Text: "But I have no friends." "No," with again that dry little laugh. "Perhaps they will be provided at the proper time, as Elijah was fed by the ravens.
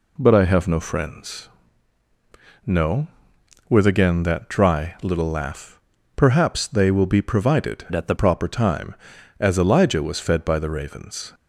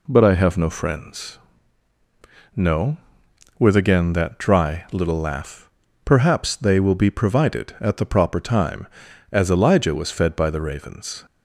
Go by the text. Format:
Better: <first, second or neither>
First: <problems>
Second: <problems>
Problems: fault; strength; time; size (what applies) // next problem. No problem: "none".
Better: second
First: changes voice from "at" to "the"; from 7.9 to 8.1 s; 0.2 s long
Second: none